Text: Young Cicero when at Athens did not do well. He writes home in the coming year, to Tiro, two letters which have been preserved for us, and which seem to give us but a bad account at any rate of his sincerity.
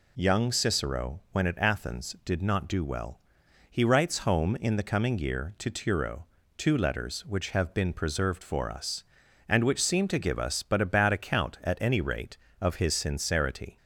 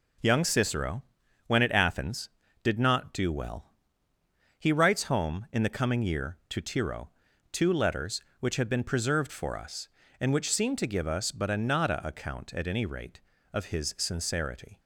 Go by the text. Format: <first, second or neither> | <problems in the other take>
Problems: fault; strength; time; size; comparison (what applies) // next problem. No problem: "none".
first | pauses between "Cicero" and "when"; noticeable; at 1.0 s; 0.46 s long // says "nada" for "bad"; at 11.5 s